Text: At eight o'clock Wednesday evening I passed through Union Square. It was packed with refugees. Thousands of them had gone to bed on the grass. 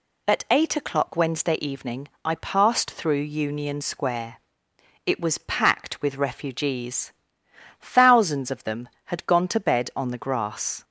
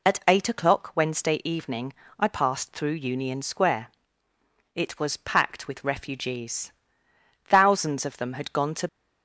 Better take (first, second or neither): first